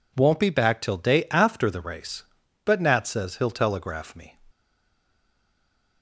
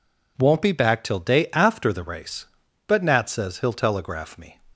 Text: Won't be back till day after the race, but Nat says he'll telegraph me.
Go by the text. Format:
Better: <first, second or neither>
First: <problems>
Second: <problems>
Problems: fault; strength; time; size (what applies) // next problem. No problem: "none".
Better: second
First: stays silent after the last word; noticeable; from 4.5 s on; 1.5 s long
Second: none